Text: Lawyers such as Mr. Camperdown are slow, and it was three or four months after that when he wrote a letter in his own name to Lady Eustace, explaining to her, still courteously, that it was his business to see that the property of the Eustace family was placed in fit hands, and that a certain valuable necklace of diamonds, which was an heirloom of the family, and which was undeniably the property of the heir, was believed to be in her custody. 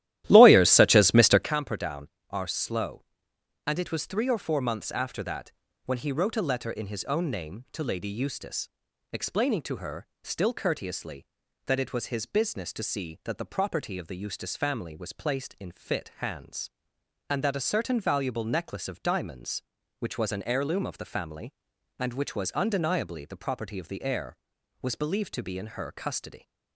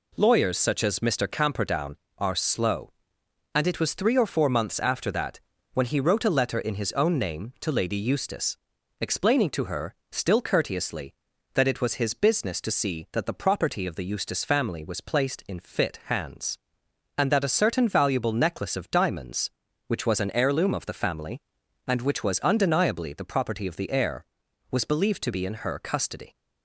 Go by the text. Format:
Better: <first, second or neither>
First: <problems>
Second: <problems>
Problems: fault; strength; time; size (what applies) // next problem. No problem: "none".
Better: second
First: starts louder than the rest; strong; until 1.5 s; 14 dB // pauses between "that" and "when"; slight; at 5.5 s; 0.34 s long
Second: pauses between "that" and "when"; slight; at 5.3 s; 0.34 s long